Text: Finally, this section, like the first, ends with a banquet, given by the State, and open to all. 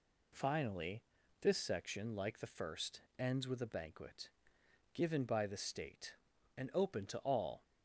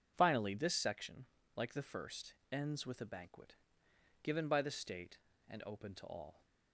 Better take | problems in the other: neither | none

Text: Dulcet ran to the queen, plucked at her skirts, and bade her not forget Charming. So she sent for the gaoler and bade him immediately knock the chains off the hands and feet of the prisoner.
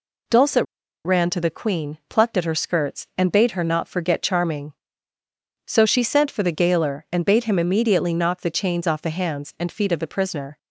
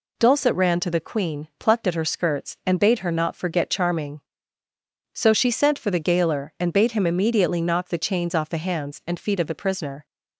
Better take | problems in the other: second | pauses between "Dulcet" and "ran"; at 0.6 s; 0.40 s long

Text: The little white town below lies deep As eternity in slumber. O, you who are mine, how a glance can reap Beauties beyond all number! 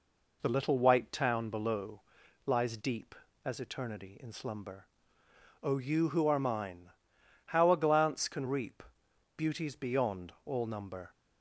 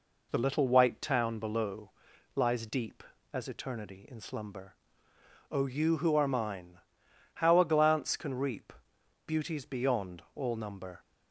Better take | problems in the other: neither | pauses between "below" and "lies"; noticeable; the same in both // pauses between "reap" and "Beauties"; noticeable; the same in both

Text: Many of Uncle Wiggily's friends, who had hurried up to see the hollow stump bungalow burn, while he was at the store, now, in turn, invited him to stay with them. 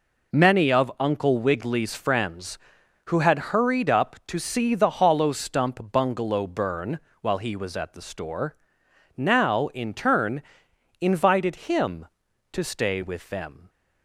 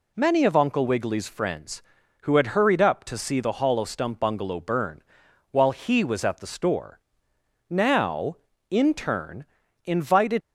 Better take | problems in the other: first | stops before "him to stay with them"; at 10.4 s

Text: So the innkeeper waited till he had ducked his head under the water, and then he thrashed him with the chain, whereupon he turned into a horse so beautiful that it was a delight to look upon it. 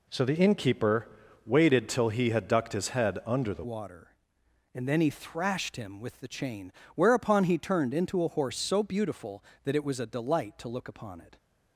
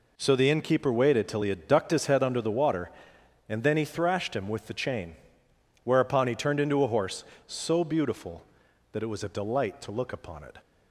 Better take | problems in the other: second | pauses between "innkeeper" and "waited"; at 1.0 s; 0.38 s long // changes voice at "water"; from 3.6 s on; 7.7 s long

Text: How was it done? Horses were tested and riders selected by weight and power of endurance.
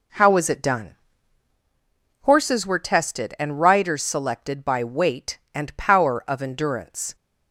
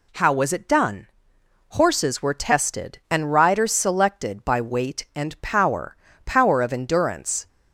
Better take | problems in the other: first | says "power" twice; at 6.2 s

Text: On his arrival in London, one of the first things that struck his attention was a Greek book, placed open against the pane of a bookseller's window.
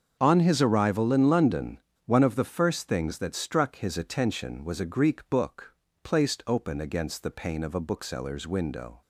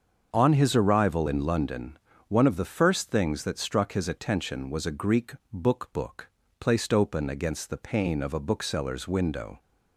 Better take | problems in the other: first | starts louder than the rest; until 1.3 s; 6.5 dB; also in the first // pauses between "Greek" and "book"; slight; at 5.3 s; 0.18 s long // says "book" twice; at 5.9 s

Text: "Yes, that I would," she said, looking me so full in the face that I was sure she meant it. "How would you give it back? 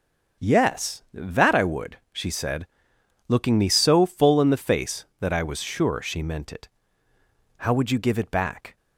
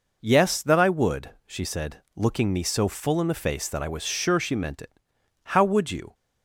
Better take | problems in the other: first | stops before "give it back"; at 6.1 s

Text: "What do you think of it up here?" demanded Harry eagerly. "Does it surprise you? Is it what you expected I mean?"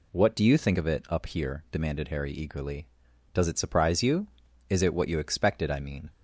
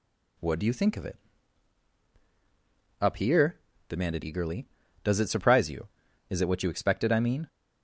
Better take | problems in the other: first | pauses between "it" and "up"; strong; at 1.1 s; 1.8 s long // skips "Harry"; at 4.2 s

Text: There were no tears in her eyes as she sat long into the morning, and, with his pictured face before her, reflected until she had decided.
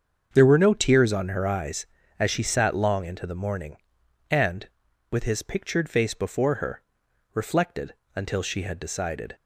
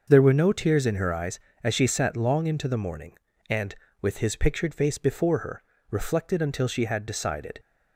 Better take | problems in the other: second | starts louder than the rest; until 1.3 s; 7 dB; also in the second // says "on" for "in"; at 1.1 s // pauses between "reflected" and "until"; slight; at 7.9 s; 0.22 s long

